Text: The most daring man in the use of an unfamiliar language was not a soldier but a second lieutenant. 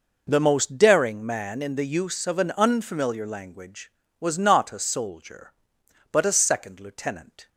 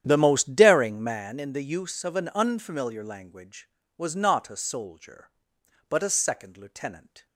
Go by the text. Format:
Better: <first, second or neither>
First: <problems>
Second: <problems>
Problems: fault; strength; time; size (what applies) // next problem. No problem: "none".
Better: first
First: none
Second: starts louder than the rest; strong; until 1.2 s; 9.5 dB